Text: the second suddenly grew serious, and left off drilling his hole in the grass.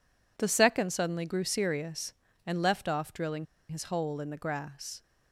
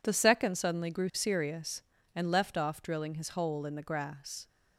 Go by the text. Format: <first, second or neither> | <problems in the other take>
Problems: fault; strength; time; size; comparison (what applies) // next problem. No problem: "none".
second | pauses between "drilling" and "his"; slight; at 3.4 s; 0.24 s long